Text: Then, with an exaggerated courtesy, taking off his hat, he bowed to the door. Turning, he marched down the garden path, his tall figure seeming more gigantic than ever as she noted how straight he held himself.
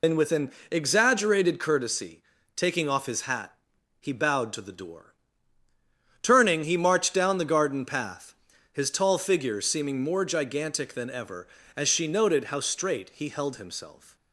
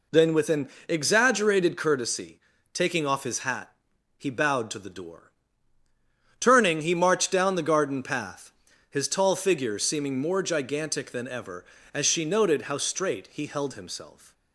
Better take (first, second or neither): second